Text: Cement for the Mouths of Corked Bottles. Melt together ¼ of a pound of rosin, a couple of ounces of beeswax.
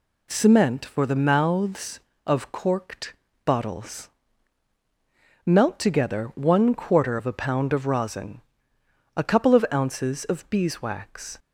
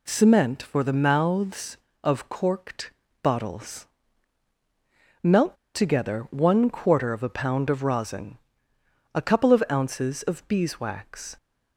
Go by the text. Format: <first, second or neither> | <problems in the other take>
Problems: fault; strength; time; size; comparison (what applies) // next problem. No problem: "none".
first | pauses between "Corked" and "Bottles"; slight; at 2.9 s; 0.30 s long; slight in the first // pauses between "Melt" and "together"; slight; at 5.5 s; 0.18 s long